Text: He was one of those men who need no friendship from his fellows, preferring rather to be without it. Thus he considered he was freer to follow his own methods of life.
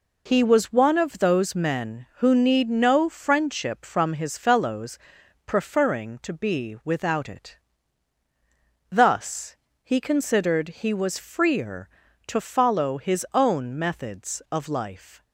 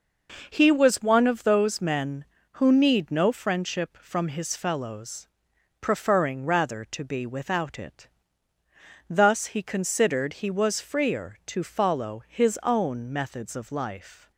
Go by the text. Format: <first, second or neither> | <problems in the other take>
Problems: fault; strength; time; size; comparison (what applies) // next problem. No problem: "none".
second | skips "rather"; at 6.2 s // pauses between "Thus" and "he"; slight; at 9.5 s; 0.30 s long